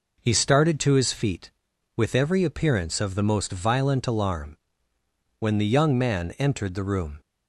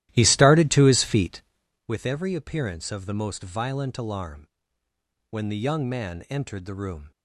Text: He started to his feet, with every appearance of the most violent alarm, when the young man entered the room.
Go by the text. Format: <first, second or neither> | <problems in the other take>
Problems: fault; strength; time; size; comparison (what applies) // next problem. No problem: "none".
first | starts louder than the rest; strong; until 1.9 s; 14 dB